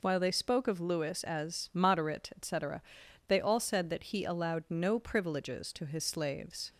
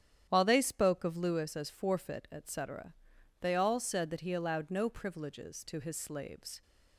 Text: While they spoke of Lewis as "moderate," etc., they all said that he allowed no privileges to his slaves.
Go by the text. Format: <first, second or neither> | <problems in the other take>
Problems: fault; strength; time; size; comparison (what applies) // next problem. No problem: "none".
first | starts louder than the rest; strong; until 1.3 s; 10 dB // says "forfeit" for "moderate"; at 1.6 s